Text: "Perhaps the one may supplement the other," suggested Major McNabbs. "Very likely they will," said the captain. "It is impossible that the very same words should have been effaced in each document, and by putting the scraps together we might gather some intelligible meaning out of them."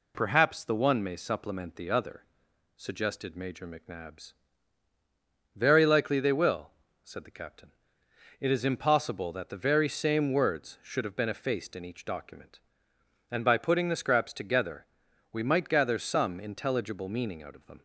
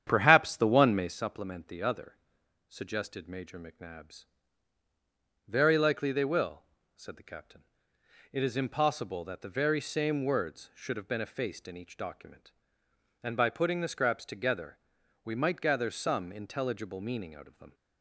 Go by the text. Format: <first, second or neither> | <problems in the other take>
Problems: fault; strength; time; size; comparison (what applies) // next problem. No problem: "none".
first | starts louder than the rest; strong; until 1.2 s; 9 dB // pauses between "together" and "we"; noticeable; at 14.7 s; 0.48 s long; noticeable in the first